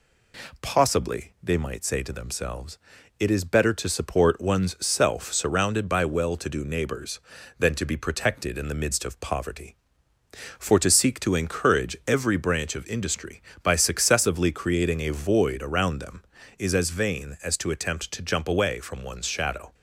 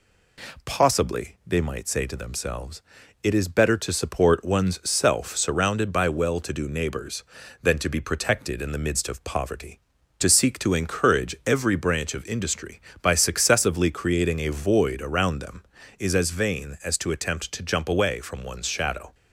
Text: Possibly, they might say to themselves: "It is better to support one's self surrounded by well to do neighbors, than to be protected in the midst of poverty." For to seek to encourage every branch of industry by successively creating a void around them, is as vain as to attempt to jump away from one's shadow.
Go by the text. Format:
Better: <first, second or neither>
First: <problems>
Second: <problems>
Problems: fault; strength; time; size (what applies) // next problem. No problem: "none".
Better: first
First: none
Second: skips "For"; at 10.0 s